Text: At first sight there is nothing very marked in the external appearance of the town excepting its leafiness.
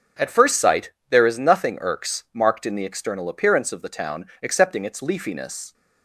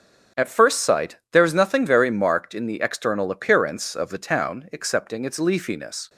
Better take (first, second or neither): second